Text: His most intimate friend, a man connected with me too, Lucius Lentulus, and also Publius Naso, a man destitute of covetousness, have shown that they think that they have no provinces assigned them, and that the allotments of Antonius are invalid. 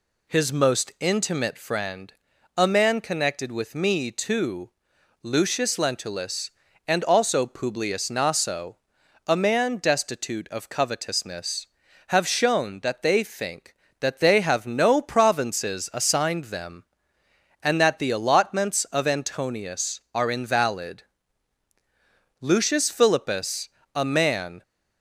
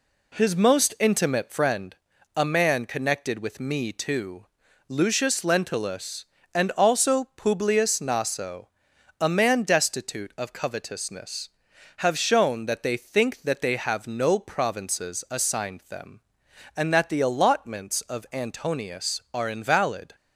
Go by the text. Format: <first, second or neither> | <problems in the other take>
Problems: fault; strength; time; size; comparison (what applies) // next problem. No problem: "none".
second | goes on to say "Lucius Philippus a man"; strong; from 22.4 s on; 2.2 s long